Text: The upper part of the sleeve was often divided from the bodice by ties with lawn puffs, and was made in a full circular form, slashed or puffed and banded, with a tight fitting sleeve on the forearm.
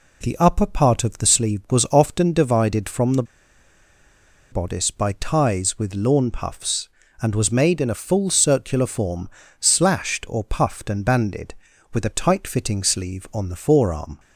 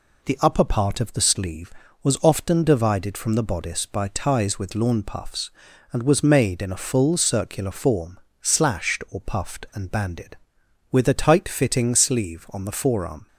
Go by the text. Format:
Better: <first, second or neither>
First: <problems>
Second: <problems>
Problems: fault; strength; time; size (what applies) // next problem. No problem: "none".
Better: second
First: pauses between "the" and "bodice"; strong; at 3.2 s; 1.2 s long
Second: none